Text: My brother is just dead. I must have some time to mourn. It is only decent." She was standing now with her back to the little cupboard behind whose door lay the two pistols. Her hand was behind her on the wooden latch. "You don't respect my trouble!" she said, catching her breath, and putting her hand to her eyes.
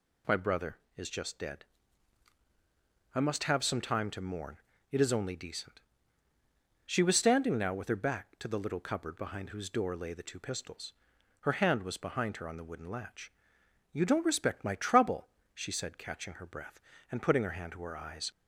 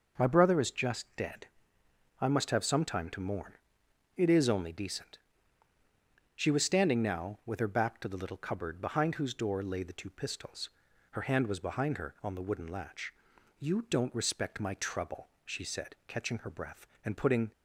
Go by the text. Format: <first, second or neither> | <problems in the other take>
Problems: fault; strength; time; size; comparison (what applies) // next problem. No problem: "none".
first | stops before "her hand to her eyes"; at 17.5 s